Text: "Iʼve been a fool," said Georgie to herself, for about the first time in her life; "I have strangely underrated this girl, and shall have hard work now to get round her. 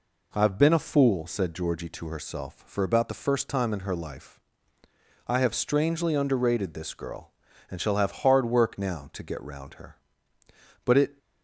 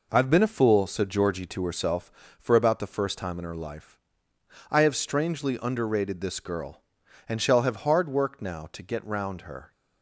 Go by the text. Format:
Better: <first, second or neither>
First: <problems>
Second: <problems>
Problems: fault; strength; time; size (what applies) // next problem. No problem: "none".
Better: second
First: goes on to say "But it"; slight; from 10.8 s on; 0.32 s long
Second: none